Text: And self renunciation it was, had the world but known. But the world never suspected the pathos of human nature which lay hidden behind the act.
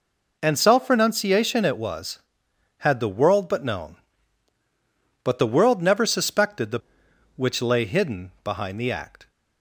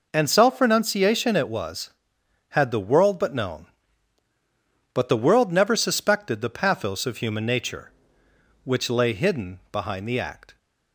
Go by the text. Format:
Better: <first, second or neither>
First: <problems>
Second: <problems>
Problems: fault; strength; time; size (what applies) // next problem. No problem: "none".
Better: second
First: skips "pathos of human nature"; at 7.0 s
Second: none